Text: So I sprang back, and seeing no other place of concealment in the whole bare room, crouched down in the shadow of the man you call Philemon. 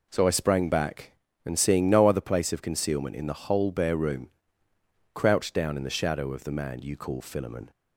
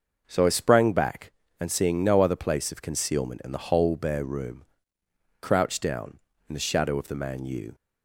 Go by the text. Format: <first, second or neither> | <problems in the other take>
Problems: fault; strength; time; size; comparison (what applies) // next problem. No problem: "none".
first | starts louder than the rest; noticeable; until 1.2 s; 6 dB // stops before "call Philemon"; at 7.7 s